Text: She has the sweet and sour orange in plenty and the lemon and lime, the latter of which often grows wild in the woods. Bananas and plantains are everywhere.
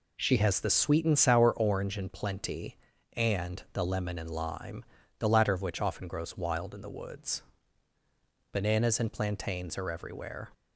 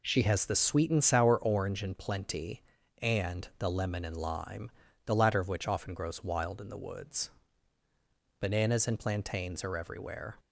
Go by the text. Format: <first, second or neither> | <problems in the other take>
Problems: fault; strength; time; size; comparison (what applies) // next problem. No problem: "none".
neither | none